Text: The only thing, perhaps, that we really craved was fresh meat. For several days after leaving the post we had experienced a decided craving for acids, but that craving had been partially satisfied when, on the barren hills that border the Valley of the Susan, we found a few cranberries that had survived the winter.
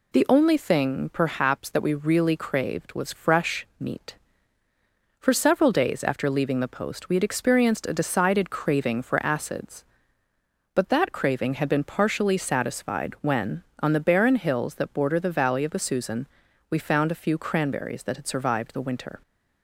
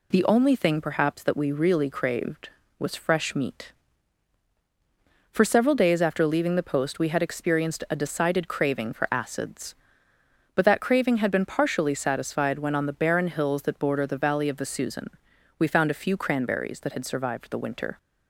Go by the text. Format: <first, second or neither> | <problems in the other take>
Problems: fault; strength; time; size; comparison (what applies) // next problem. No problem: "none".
neither | none